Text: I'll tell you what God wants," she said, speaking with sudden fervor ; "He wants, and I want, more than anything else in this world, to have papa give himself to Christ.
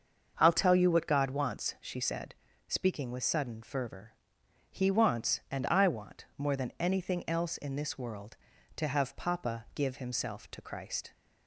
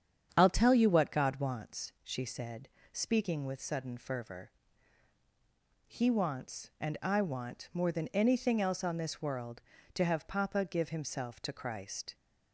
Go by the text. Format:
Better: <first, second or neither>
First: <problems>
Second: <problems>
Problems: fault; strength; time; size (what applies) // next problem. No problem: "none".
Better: first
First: starts louder than the rest; until 1.3 s; 6.5 dB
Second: starts louder than the rest; strong; until 1.3 s; 8 dB // says "on" for "in"; at 8.8 s